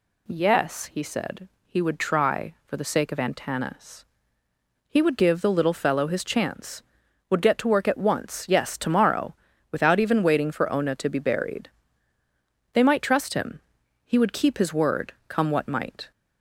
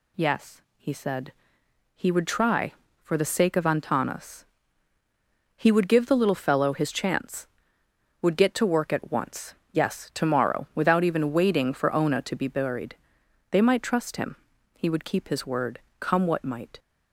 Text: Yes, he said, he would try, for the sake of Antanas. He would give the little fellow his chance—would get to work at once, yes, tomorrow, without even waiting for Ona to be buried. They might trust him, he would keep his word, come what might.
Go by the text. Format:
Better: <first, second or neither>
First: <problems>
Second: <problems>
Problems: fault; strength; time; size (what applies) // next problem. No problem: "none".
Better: neither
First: none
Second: none